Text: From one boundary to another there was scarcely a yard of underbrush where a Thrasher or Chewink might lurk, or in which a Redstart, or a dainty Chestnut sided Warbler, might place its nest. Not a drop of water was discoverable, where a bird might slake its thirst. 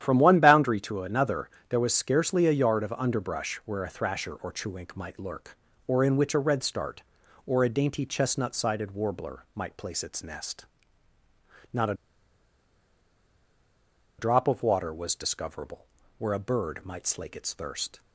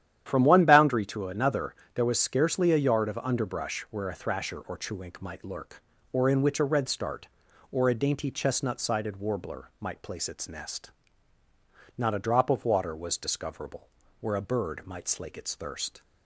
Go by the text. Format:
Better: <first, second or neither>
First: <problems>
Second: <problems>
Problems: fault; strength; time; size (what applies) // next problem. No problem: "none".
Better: second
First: starts louder than the rest; strong; until 1.0 s; 10.5 dB // pauses between "another" and "there"; slight; at 1.4 s; 0.22 s long // pauses between "a" and "drop"; strong; at 11.9 s; 2.2 s long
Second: starts louder than the rest; strong; until 1.2 s; 10.5 dB // pauses between "another" and "there"; slight; at 1.7 s; 0.22 s long